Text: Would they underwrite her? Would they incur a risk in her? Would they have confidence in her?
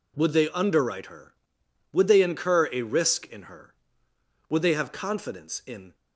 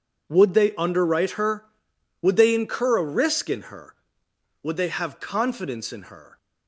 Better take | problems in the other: second | stops before "her"; at 5.9 s

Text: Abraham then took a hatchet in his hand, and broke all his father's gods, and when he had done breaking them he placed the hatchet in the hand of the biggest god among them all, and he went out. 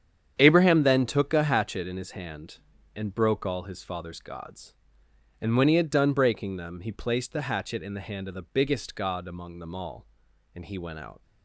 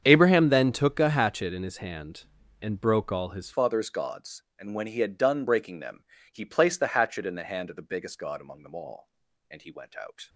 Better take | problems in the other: first | starts louder than the rest; strong; until 1.0 s; 8 dB; strong in the first // changes voice at "father's"; from 3.5 s on; 6.7 s long // pauses between "them" and "he"; slight; at 6.0 s; 0.30 s long

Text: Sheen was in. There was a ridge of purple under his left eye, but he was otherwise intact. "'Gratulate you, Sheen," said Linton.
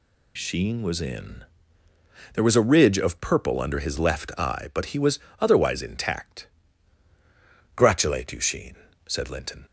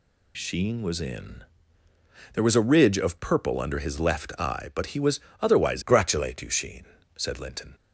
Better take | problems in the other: first | pauses between "was" and "otherwise"; slight; at 5.1 s; 0.20 s long; slight in the first // skips "intact"; at 5.8 s

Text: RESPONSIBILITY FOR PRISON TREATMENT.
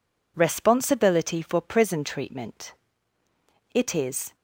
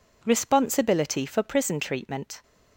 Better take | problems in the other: second | goes on to say "It is"; noticeable; from 3.7 s on; 0.62 s long

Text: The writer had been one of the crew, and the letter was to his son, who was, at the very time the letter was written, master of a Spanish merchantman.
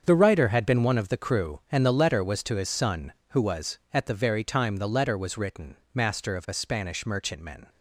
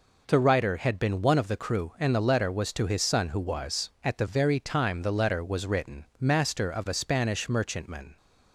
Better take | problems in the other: second | gets quieter; strong; throughout; 11 dB

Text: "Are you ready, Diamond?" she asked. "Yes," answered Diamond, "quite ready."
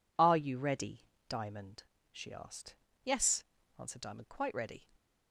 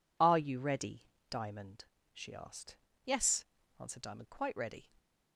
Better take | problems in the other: neither | none

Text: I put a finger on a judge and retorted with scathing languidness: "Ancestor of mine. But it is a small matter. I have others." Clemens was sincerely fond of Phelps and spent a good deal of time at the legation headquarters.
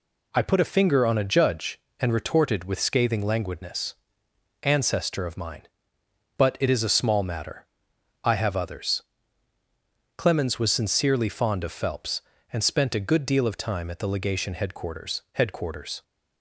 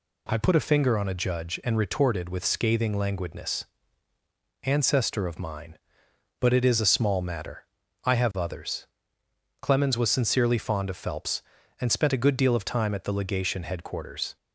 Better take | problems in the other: second | says "headquarters" twice; at 15.3 s

